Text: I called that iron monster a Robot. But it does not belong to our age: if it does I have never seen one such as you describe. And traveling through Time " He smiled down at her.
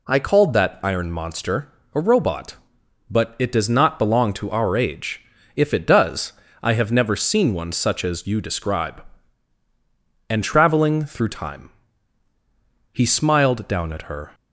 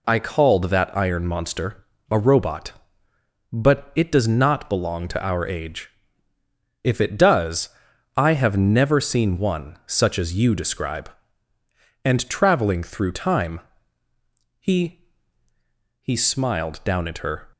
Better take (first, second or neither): first